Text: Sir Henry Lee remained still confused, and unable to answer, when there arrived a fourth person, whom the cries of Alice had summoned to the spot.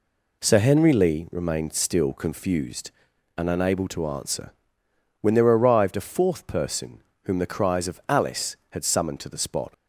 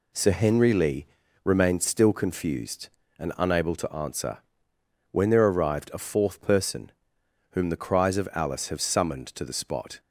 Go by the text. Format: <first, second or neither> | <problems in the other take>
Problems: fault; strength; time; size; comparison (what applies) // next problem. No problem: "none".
first | pauses between "Lee" and "remained"; at 1.0 s; 0.38 s long // says "have" for "had"; at 8.6 s